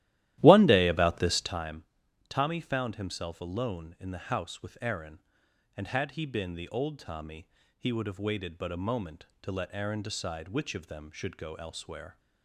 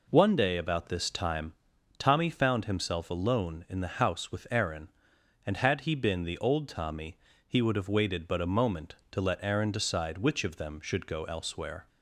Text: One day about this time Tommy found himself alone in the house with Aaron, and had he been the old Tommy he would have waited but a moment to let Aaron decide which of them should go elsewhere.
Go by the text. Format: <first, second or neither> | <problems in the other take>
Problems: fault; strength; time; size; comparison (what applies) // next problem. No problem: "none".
second | starts louder than the rest; strong; until 1.6 s; 14.5 dB // pauses between "time" and "Tommy"; noticeable; at 1.8 s; 0.46 s long; noticeable in the second // pauses between "Tommy" and "he"; slight; at 7.4 s; 0.28 s long; slight in the second